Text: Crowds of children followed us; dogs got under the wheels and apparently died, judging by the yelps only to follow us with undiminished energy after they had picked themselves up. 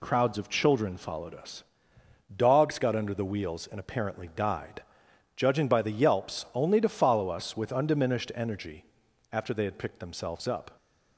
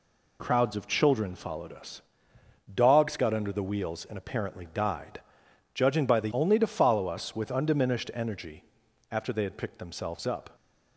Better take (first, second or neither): first